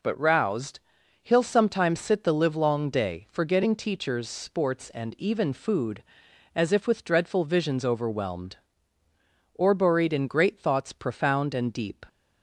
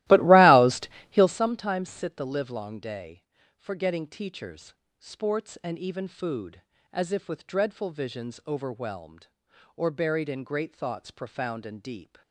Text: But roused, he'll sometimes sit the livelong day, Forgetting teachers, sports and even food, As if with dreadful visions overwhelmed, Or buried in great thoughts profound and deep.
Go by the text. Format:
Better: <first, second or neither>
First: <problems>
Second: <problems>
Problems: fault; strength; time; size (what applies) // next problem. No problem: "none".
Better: first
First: none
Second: starts louder than the rest; strong; until 1.4 s; 17 dB